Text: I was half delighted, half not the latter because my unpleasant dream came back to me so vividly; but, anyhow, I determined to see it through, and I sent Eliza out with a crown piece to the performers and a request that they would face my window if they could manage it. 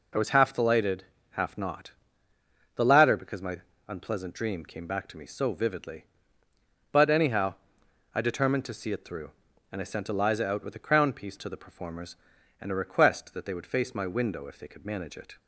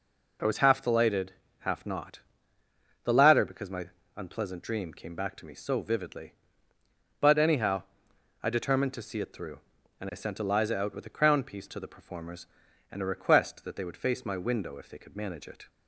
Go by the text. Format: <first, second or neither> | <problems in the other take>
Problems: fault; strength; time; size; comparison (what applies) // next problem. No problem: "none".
neither | pauses between "not" and "the"; noticeable; the same in both // pauses between "my" and "unpleasant"; slight; the same in both